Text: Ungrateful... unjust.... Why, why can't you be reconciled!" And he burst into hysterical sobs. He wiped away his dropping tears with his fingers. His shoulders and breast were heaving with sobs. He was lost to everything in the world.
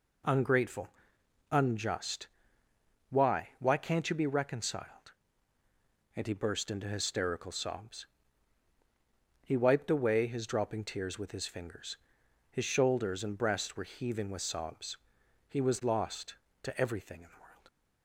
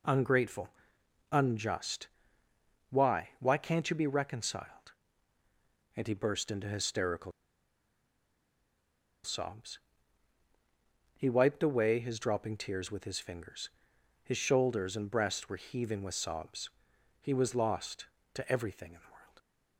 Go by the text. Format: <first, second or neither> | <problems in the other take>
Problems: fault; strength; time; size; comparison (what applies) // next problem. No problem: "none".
first | pauses between "hysterical" and "sobs"; strong; at 7.3 s; 1.9 s long